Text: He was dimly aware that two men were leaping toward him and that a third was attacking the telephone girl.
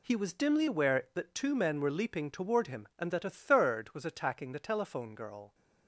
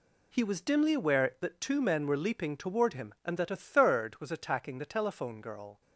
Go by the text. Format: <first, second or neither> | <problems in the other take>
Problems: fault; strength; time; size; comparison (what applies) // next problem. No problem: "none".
neither | none